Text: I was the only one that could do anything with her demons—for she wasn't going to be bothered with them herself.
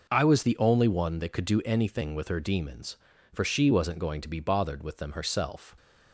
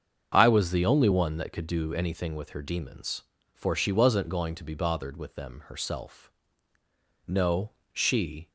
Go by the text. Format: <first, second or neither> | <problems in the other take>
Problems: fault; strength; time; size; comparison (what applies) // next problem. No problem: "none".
first | starts louder than the rest; until 1.3 s; 7 dB // goes on to say "No she"; noticeable; from 7.2 s on; 1.2 s long